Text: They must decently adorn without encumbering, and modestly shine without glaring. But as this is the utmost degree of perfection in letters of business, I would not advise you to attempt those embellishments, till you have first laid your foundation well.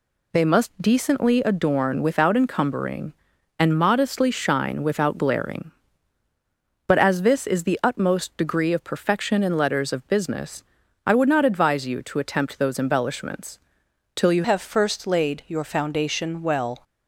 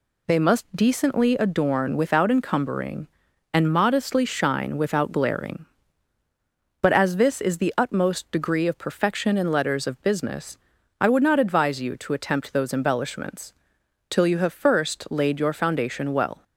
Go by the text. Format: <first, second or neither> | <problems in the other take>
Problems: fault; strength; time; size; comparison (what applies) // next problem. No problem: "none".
second | changes voice at "have"; from 14.4 s on; 2.4 s long